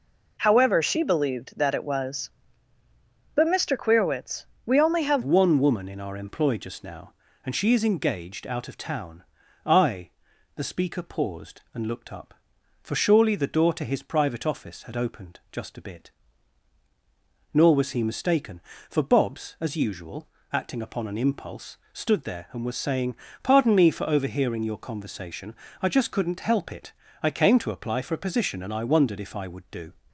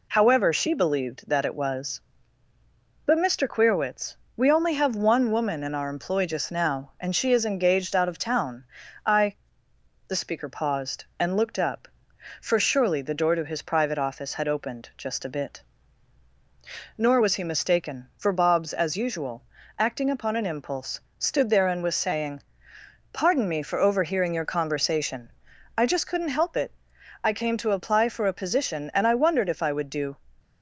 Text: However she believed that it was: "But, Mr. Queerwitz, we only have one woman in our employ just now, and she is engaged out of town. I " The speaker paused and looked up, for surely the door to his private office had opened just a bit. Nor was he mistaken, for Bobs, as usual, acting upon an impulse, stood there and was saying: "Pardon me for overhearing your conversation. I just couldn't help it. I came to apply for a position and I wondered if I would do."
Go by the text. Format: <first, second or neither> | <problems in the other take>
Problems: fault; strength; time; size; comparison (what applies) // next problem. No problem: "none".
second | changes voice at "one"; from 5.2 s on; 24.7 s long